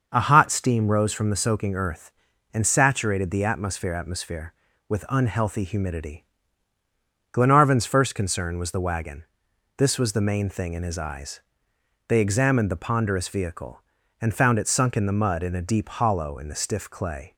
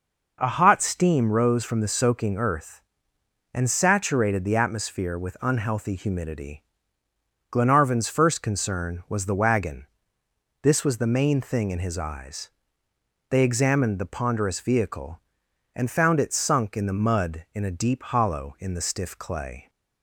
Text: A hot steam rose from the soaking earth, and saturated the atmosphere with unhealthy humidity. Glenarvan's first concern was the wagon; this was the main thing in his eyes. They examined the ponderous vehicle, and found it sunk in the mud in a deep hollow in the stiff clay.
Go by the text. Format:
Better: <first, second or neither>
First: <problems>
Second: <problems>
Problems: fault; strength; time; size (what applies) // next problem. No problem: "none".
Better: second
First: starts louder than the rest; until 1.1 s; 6.5 dB // says "atmosphere" twice; at 3.9 s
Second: none